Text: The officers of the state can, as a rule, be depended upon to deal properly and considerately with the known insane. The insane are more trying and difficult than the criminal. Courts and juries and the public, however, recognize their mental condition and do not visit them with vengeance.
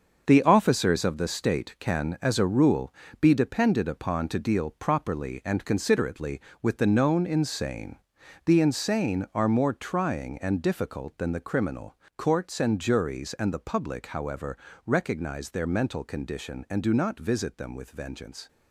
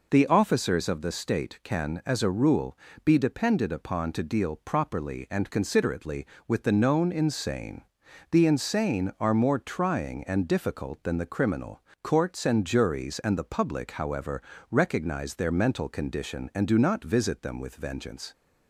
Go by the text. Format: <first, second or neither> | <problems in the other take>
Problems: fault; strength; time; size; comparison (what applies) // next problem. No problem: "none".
second | gets quieter; strong; throughout; 9 dB